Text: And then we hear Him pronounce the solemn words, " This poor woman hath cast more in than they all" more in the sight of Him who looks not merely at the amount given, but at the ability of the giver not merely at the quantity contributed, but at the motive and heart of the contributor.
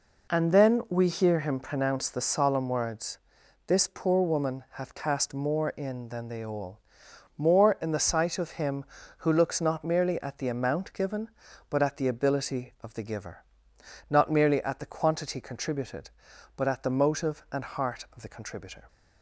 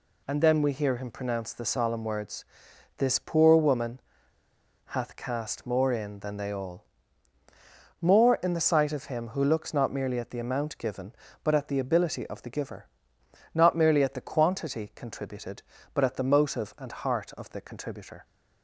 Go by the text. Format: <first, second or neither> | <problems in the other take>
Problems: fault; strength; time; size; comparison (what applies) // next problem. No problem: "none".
first | pauses between "woman" and "hath"; noticeable; at 3.9 s; 0.87 s long // pauses between "all" and "more"; at 6.8 s; 1.1 s long; noticeable in the first // pauses between "giver" and "not"; noticeable; at 12.8 s; 0.66 s long; noticeable in the first